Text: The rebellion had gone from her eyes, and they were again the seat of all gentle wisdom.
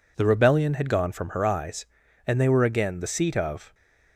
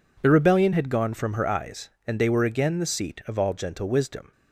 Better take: second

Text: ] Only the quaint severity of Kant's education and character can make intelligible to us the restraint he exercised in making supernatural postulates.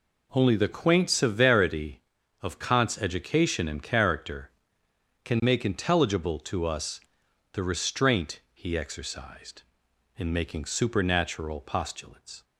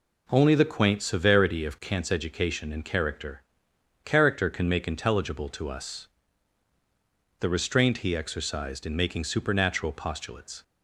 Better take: first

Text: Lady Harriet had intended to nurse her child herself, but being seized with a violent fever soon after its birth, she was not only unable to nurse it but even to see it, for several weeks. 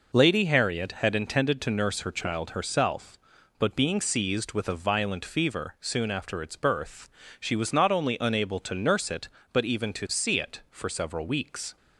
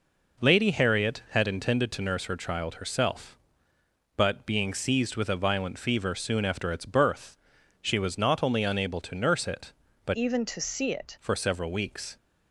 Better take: first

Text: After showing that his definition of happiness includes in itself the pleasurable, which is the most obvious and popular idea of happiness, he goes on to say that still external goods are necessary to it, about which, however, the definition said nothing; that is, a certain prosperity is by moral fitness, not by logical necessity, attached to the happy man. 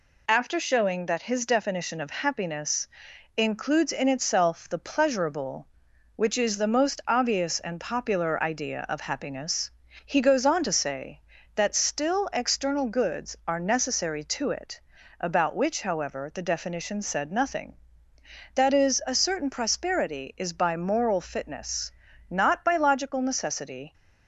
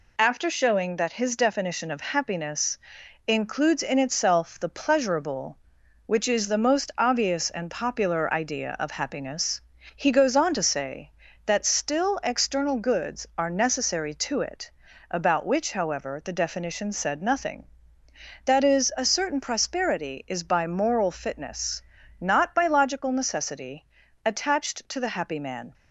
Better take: second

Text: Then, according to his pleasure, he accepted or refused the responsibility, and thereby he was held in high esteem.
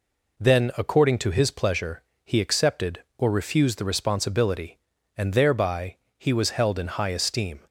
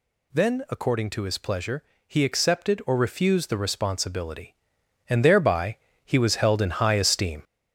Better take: first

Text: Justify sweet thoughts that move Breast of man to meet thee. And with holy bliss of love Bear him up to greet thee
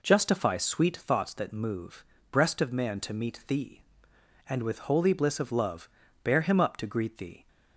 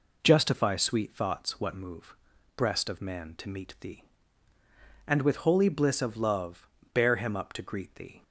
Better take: first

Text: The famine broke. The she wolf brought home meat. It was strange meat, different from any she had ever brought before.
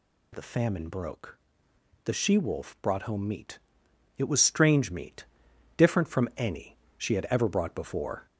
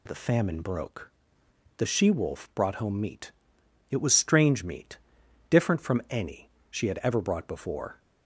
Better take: second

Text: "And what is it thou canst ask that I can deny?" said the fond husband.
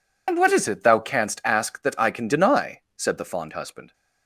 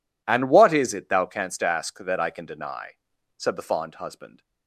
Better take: second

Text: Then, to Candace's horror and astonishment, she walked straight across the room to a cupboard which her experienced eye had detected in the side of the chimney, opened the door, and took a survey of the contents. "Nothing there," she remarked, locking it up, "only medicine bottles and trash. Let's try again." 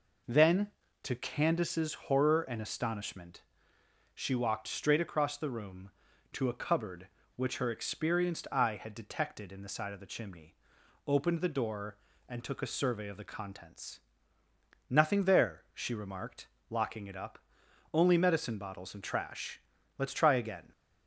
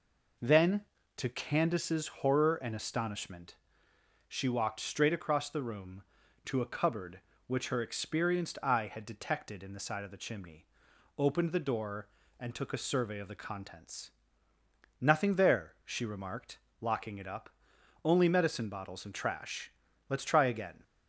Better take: neither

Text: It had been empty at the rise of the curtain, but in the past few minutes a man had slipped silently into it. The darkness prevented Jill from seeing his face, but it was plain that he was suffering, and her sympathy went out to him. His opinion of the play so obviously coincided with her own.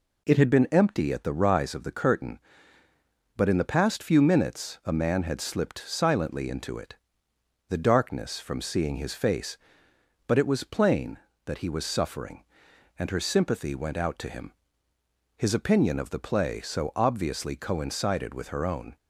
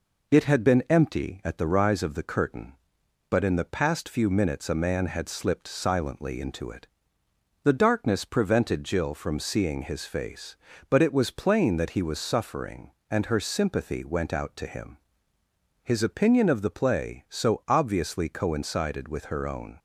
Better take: second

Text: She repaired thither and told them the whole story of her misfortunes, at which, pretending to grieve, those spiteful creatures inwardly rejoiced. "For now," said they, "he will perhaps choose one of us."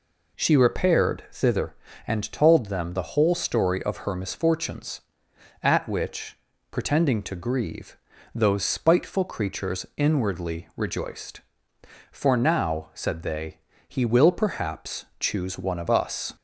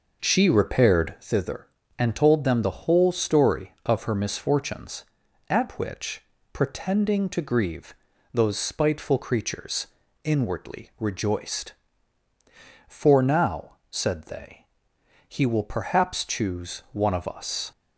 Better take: first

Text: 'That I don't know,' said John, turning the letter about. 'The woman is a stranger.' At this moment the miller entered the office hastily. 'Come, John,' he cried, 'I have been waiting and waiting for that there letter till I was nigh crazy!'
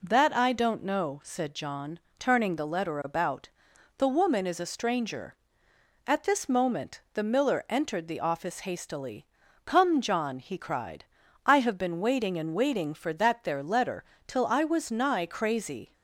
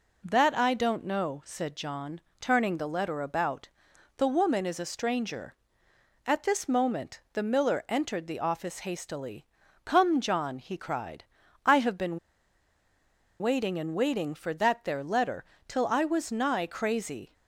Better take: first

